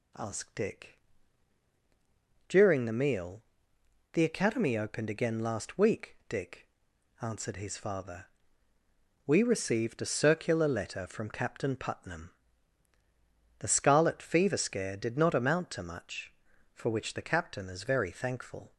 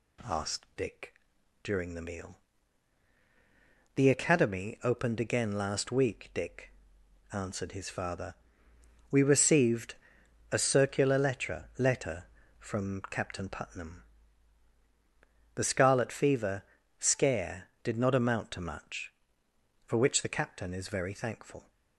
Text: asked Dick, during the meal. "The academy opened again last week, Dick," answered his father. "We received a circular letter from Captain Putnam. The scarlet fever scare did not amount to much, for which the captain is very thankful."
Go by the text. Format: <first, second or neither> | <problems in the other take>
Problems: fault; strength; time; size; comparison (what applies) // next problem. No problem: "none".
first | pauses between "received" and "a"; noticeable; at 9.9 s; 0.56 s long // says "letter" twice; at 11.7 s // pauses between "fever" and "scare"; slight; at 16.6 s; 0.36 s long